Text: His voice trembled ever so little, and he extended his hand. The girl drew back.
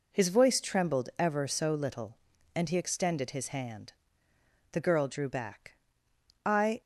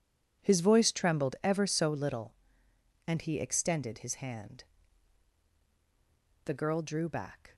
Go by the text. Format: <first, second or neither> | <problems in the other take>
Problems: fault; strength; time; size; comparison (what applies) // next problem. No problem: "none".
second | goes on to say "I"; slight; from 6.4 s on; 0.36 s long